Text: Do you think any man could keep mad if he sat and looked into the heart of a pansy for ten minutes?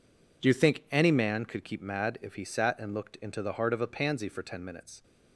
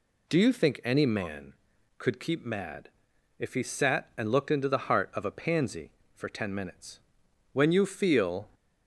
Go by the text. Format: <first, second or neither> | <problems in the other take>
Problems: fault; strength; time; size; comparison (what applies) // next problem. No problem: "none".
first | pauses between "mad" and "if"; noticeable; at 2.8 s; 0.50 s long // goes on to say "When you feel"; noticeable; from 7.5 s on; 0.96 s long